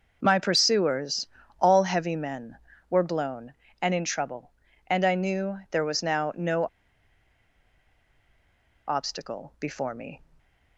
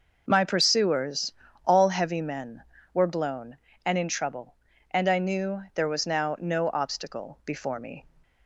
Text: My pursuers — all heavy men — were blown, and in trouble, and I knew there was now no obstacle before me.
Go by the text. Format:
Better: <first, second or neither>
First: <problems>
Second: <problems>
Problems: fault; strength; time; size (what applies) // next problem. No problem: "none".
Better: second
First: pauses between "no" and "obstacle"; strong; at 6.6 s; 2.2 s long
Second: none